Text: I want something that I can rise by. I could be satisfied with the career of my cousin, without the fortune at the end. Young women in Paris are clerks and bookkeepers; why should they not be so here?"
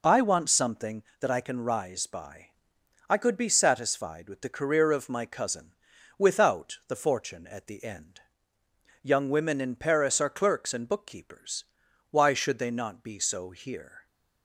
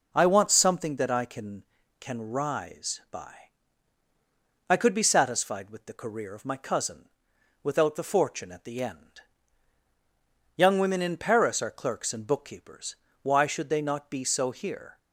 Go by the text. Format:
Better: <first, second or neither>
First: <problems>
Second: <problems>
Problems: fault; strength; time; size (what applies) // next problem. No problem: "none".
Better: first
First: none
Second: says "can" twice; at 1.9 s